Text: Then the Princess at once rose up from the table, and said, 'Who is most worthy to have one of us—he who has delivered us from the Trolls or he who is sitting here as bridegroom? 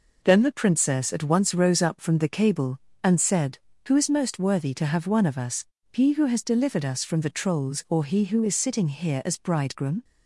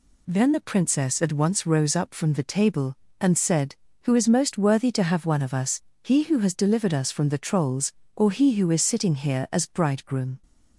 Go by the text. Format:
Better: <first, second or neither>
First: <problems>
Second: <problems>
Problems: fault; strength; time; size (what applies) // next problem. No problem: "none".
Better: second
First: says "cable" for "table"; at 2.2 s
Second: none